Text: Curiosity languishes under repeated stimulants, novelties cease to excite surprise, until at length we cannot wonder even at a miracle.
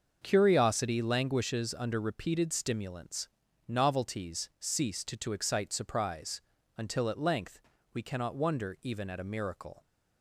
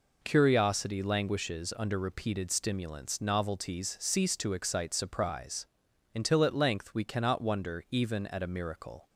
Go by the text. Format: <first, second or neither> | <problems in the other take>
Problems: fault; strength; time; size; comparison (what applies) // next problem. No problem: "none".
second | starts louder than the rest; until 1.2 s; 6.5 dB // says "to" twice; at 5.1 s // pauses between "length" and "we"; slight; at 7.6 s; 0.32 s long